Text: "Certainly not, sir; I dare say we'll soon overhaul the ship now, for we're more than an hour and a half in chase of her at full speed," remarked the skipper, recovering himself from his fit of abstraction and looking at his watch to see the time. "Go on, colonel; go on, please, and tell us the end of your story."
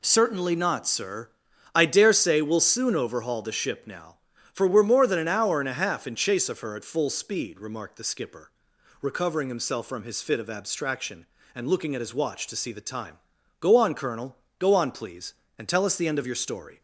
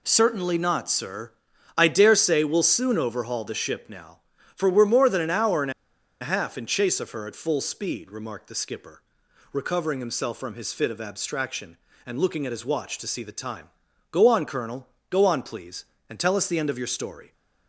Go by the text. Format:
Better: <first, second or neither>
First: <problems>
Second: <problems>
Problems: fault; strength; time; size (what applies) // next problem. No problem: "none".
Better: first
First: none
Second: pauses between "and" and "a"; noticeable; at 5.7 s; 0.50 s long